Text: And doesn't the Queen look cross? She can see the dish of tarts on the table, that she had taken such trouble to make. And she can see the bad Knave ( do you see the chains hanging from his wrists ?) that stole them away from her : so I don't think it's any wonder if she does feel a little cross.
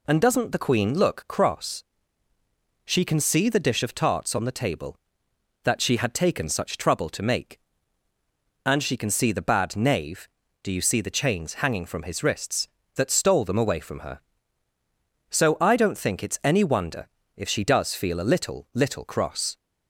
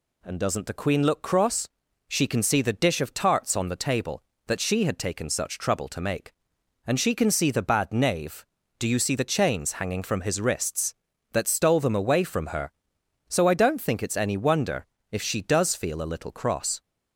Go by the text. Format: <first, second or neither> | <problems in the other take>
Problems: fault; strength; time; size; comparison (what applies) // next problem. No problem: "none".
second | pauses between "wonder" and "if"; slight; at 17.0 s; 0.28 s long; slight in the second // says "little" twice; at 18.7 s